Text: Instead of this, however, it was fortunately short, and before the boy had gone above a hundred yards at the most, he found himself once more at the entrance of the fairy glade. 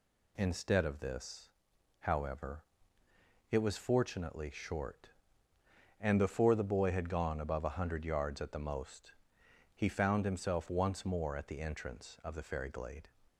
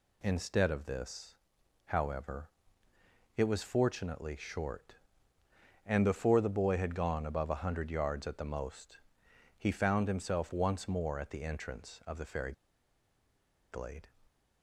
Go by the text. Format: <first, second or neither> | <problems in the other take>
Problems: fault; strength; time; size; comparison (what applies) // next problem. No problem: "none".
first | pauses between "fairy" and "glade"; at 12.5 s; 1.1 s long